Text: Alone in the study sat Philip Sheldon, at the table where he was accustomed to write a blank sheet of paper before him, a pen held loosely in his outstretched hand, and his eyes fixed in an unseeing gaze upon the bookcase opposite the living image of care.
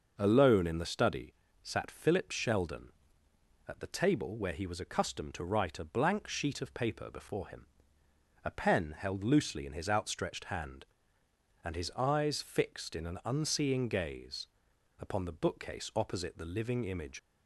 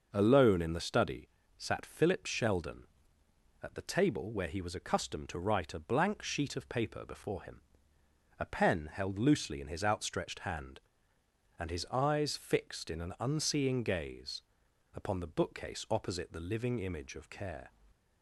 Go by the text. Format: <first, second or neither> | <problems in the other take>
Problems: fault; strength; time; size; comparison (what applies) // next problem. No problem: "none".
second | pauses between "study" and "sat"; slight; at 1.3 s; 0.30 s long; slight in the second // pauses between "gaze" and "upon"; noticeable; at 14.4 s; 0.54 s long; noticeable in the second // stops before "of care"; at 17.1 s